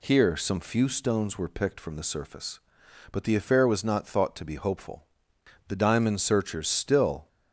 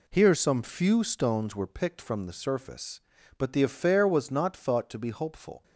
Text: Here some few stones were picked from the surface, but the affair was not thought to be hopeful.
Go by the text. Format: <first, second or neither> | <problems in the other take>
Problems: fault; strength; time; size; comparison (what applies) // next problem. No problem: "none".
second | goes on to say "The diamond searchers still"; from 5.6 s on; 1.6 s long